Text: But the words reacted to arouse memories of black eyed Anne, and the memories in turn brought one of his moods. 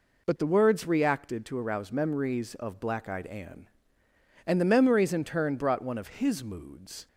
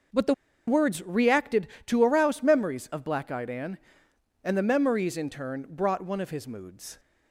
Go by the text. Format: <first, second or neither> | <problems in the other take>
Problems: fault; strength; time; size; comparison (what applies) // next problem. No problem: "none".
first | pauses between "the" and "words"; slight; at 0.3 s; 0.33 s long